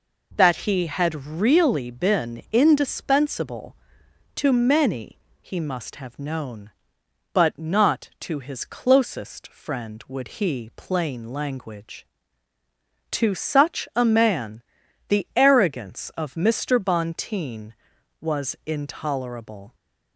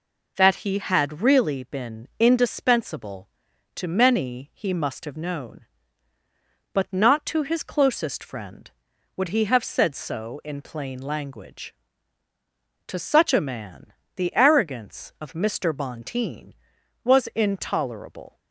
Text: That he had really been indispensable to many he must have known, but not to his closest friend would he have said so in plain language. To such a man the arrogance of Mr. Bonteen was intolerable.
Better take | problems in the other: second | pauses between "many" and "he"; slight; at 5.1 s; 0.22 s long // skips "have said so in"; at 10.7 s // pauses between "man" and "the"; noticeable; at 14.6 s; 0.46 s long; slight in the second

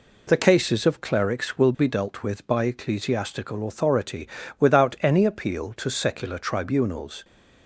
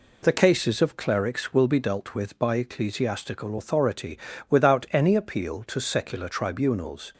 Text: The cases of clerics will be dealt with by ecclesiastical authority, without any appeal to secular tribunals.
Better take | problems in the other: neither | none

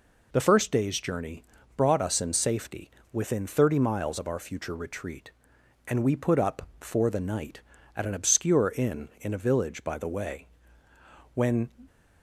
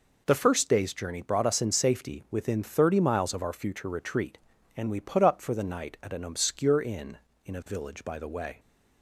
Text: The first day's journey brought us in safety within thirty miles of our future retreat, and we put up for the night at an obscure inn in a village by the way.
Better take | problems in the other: second | pauses between "journey" and "brought"; slight; at 1.4 s; 0.36 s long // pauses between "safety" and "within"; slight; at 2.8 s; 0.24 s long // goes on to say "When"; slight; from 11.3 s on; 0.36 s long

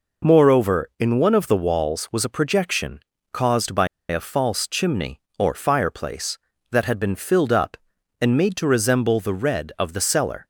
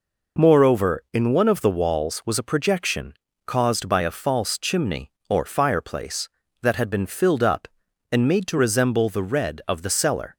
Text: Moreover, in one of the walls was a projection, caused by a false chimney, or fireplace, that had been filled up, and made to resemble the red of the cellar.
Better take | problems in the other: second | pauses between "by" and "a"; slight; at 3.8 s; 0.23 s long

